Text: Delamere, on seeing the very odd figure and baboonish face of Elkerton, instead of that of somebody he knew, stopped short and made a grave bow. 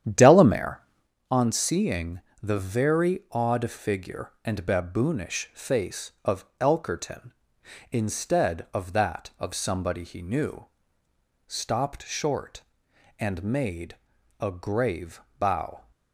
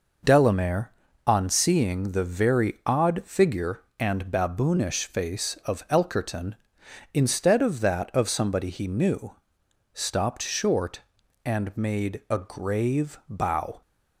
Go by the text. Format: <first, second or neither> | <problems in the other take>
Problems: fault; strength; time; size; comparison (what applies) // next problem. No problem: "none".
second | starts louder than the rest; strong; until 1.1 s; 10 dB // pauses between "seeing" and "the"; slight; at 2.2 s; 0.20 s long // pauses between "made" and "a"; at 13.9 s; 0.42 s long // pauses between "grave" and "bow"; slight; at 15.2 s; 0.20 s long